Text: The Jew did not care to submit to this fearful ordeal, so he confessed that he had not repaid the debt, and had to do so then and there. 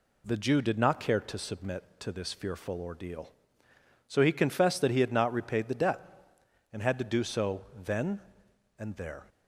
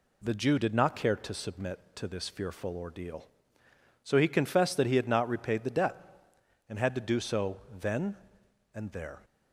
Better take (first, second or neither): neither